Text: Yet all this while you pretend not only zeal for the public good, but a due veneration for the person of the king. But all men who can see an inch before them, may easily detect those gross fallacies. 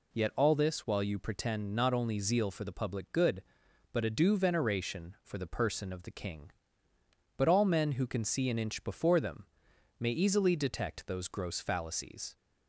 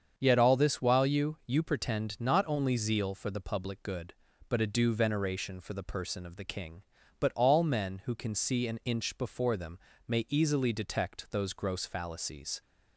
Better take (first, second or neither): first